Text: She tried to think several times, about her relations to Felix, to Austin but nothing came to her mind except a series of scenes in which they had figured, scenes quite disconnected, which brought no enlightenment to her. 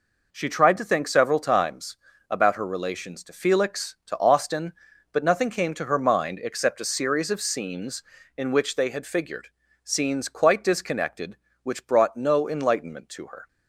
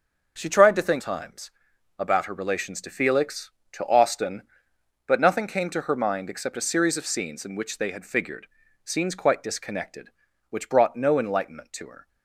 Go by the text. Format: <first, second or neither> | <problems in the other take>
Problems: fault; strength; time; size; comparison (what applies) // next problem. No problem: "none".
first | skips "several"; at 0.9 s